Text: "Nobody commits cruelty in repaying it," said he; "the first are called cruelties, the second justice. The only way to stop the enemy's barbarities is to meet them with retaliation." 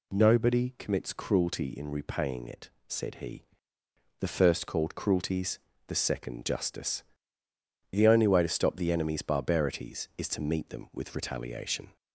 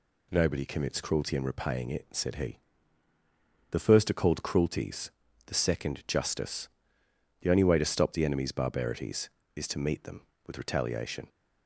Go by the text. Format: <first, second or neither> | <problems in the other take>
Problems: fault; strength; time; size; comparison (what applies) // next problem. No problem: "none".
second | skips "are"; at 4.6 s